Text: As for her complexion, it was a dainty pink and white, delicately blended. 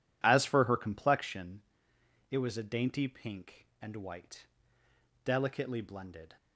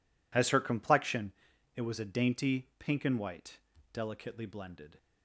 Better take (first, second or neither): first